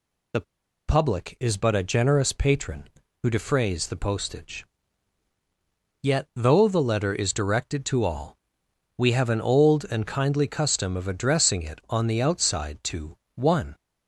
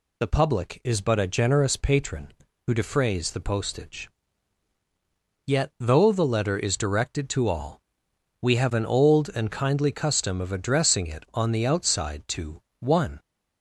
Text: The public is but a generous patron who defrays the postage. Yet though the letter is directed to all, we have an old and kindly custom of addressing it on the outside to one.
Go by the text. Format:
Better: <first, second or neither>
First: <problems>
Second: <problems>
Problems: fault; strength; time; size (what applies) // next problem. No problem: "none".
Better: second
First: pauses between "The" and "public"; noticeable; at 0.4 s; 0.47 s long // pauses between "to" and "one"; slight; at 13.1 s; 0.18 s long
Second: pauses between "to" and "one"; slight; at 12.6 s; 0.18 s long